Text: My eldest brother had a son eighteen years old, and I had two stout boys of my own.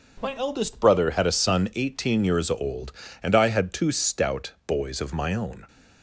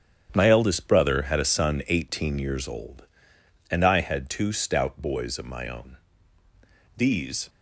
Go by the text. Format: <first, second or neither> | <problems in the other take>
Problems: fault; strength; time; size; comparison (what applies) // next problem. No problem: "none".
first | starts louder than the rest; strong; until 1.3 s; 8.5 dB // goes on to say "These"; from 6.9 s on; 0.54 s long